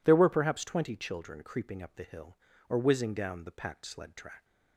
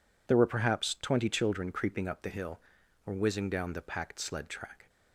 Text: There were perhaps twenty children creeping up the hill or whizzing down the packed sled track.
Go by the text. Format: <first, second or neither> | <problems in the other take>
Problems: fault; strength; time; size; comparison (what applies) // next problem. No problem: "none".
neither | none